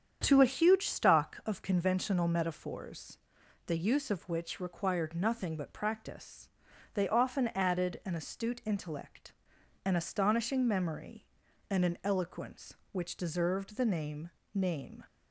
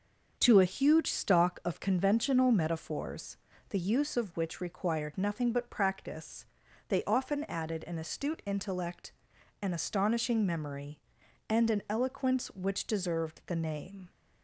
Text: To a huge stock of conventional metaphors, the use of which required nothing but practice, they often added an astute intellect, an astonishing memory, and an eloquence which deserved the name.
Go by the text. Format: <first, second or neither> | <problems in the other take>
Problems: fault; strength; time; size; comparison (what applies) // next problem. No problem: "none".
second | starts louder than the rest; strong; until 1.2 s; 8 dB; also in the second // says "name" twice; at 14.5 s